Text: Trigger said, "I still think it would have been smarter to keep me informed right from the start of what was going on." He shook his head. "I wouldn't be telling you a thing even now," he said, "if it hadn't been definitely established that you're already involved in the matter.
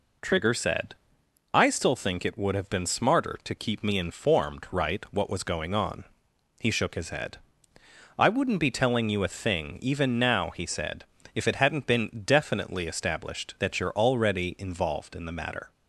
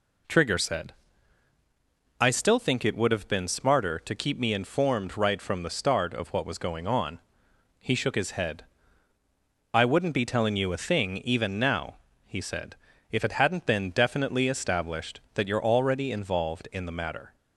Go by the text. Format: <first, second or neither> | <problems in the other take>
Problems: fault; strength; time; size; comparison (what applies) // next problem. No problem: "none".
second | skips "from the start of"; at 5.0 s